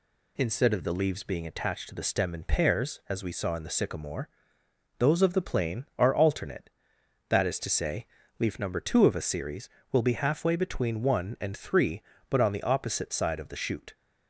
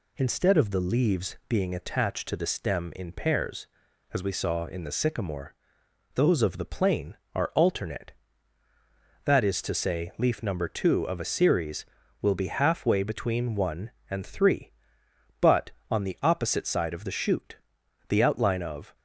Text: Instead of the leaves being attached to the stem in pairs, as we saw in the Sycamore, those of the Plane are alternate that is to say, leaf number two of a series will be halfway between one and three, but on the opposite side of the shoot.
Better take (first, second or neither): first